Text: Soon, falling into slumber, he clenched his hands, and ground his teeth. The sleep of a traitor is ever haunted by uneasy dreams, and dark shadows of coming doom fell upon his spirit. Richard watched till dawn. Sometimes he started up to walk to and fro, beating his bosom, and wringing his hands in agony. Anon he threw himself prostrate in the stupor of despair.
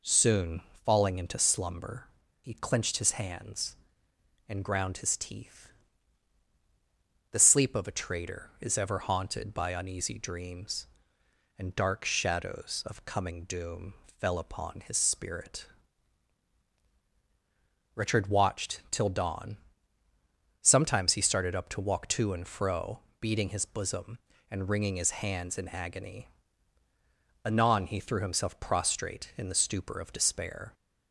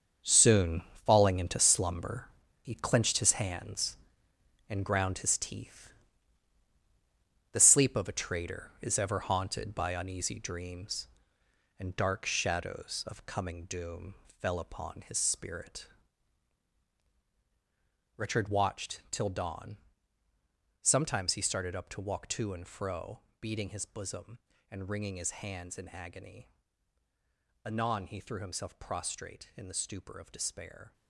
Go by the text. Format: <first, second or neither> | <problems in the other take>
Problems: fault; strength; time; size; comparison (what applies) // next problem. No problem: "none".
first | gets quieter; strong; throughout; 10.5 dB // pauses between "doom" and "fell"; slight; at 14.1 s; 0.24 s long; slight in the first